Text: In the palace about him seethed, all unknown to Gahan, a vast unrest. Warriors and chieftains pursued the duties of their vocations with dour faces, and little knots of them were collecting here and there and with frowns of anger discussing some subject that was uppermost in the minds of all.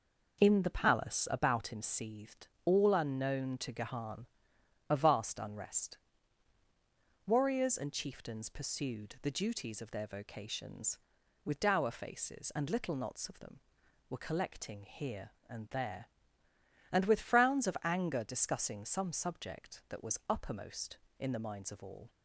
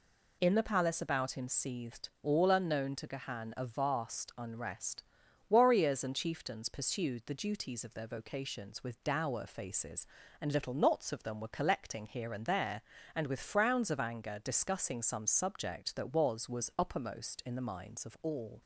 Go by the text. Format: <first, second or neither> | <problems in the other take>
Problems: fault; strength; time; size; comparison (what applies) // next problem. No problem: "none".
first | says "was" twice; at 16.4 s